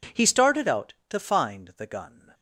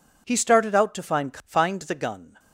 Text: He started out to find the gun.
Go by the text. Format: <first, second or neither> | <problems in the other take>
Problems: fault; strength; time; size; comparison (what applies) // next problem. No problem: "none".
first | says "find" twice; at 1.4 s